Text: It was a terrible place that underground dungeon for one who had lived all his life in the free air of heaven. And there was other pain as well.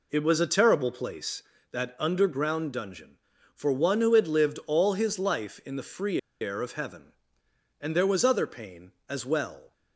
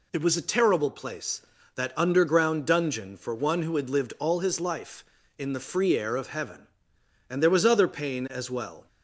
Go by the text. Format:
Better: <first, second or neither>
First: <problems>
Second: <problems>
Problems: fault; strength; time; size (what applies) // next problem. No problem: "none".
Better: second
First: pauses between "free" and "air"; slight; at 6.1 s; 0.21 s long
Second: none